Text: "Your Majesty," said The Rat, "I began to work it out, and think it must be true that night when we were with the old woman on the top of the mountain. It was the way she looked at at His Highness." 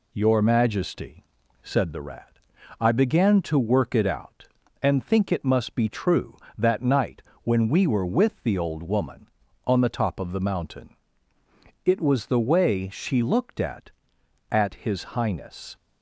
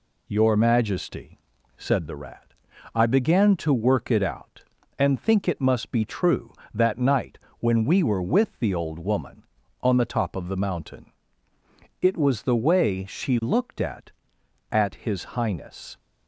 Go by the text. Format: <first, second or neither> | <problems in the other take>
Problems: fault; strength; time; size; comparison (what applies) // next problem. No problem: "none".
neither | pauses between "night" and "when"; slight; the same in both